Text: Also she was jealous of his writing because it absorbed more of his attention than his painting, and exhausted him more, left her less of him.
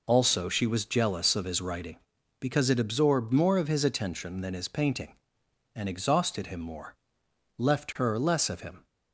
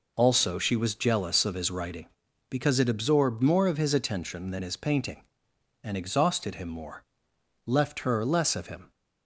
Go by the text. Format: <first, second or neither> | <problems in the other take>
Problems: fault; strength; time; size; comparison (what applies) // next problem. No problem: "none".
neither | none